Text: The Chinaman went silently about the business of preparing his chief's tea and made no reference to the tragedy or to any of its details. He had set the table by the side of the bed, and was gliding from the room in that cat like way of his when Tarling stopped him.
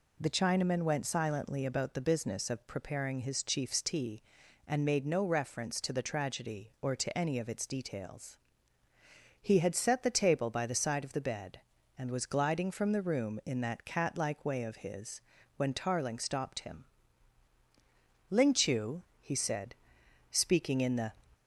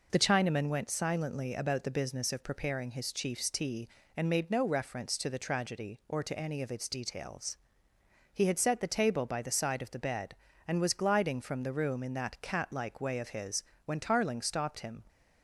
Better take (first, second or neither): second